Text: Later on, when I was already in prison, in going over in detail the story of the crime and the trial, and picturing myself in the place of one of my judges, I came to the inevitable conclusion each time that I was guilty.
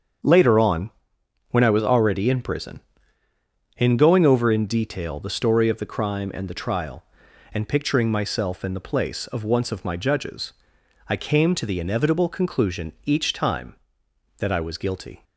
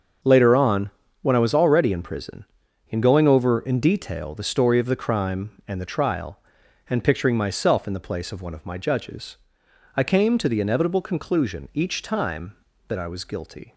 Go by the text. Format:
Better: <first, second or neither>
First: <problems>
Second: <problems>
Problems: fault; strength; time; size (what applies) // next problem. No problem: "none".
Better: second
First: starts louder than the rest; strong; until 1.8 s; 7.5 dB // says "once" for "one"; at 9.4 s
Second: starts louder than the rest; until 1.5 s; 7 dB